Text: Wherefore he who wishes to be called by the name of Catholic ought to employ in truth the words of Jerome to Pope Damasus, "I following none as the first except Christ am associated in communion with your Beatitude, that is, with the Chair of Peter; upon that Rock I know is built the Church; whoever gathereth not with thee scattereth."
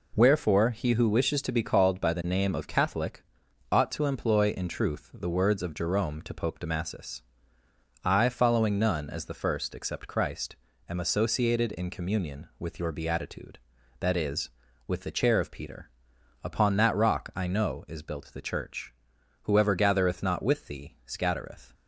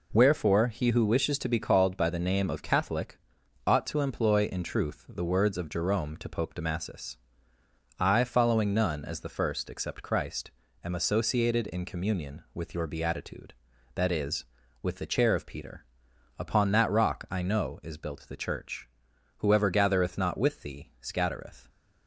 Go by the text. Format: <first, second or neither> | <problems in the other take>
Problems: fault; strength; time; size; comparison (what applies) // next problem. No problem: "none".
neither | pauses between "Catholic" and "ought"; noticeable; the same in both // pauses between "Christ" and "am"; slight; the same in both